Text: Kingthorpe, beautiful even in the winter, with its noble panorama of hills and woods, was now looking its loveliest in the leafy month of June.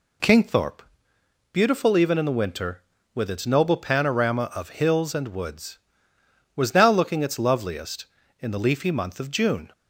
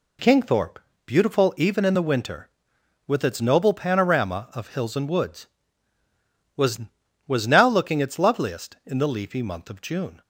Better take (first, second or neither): first